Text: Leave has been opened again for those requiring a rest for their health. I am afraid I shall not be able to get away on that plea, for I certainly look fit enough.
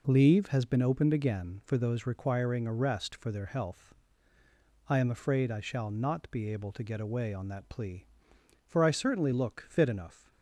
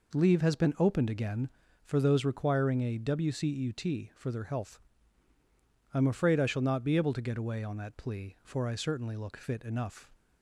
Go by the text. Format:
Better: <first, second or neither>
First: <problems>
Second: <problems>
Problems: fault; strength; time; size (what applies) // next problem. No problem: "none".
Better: first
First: none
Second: says "wcut" for "rest"; at 2.9 s